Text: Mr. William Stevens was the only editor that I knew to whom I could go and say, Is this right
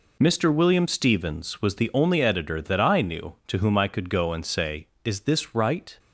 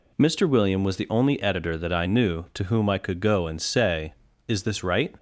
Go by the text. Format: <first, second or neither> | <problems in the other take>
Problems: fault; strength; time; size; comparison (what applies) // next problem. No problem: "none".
first | skips "Stevens"; at 0.8 s